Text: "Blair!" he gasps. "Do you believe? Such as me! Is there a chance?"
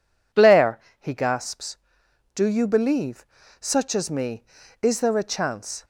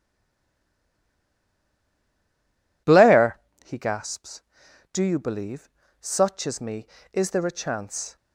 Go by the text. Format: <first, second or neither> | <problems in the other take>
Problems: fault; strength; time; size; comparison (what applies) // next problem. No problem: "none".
first | stays silent before the first word; strong; until 2.8 s; 2.8 s long